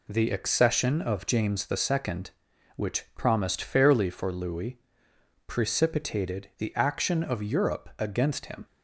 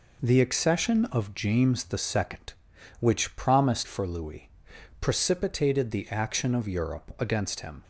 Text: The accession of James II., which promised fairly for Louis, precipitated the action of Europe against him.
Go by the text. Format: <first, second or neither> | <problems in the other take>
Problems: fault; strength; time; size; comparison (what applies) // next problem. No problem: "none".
first | skips "fairly"; at 3.8 s